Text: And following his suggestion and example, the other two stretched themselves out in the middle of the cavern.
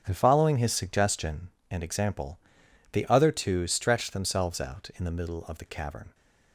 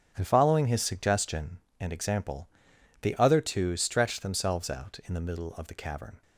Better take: neither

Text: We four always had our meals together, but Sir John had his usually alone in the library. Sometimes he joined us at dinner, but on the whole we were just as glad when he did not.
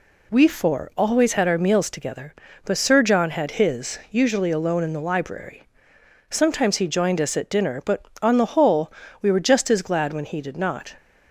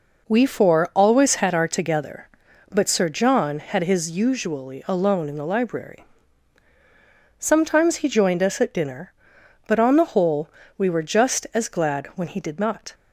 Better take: first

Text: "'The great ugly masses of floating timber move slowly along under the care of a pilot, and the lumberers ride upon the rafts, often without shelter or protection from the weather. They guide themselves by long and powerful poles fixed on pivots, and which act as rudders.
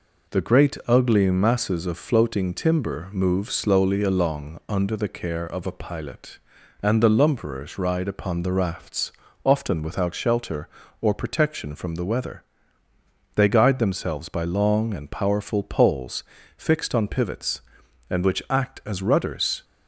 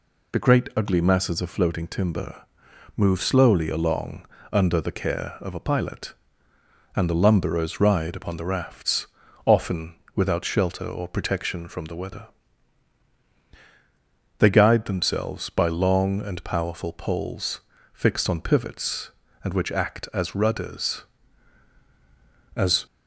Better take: first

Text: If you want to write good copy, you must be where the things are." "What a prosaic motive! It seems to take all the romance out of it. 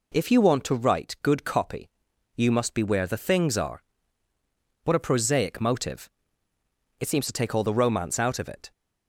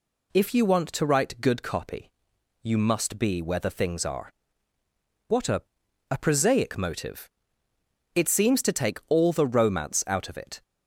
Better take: first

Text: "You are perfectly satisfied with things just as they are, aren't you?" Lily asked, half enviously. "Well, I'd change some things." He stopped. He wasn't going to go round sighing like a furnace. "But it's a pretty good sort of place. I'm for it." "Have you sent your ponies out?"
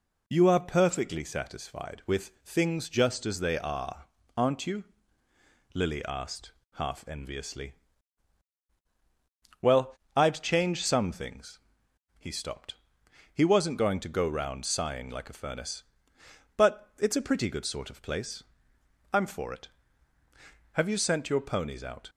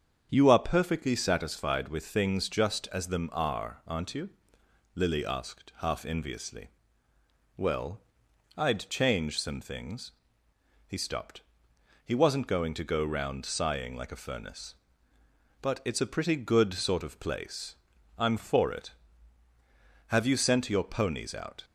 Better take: first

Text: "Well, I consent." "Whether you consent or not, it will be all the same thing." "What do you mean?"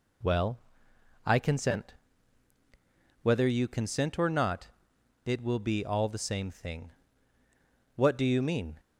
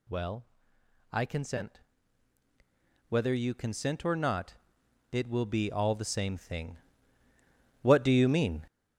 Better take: first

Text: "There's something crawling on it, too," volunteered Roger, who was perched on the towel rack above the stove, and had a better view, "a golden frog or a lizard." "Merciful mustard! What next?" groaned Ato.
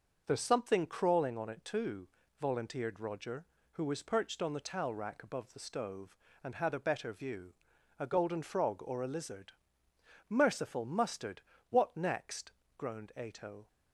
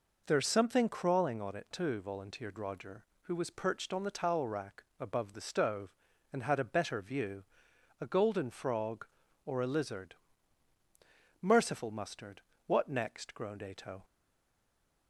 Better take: first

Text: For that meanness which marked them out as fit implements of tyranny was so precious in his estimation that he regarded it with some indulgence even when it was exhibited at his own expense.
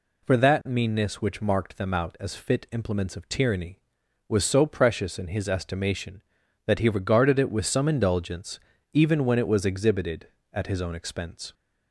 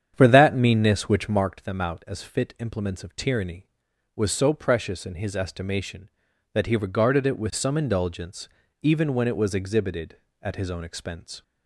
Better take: first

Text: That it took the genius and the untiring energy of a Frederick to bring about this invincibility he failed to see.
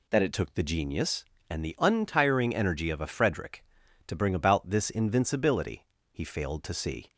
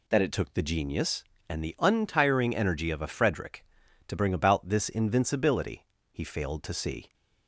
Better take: neither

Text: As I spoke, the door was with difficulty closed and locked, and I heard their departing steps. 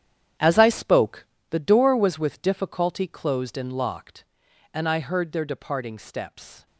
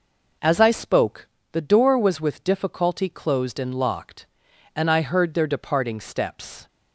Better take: second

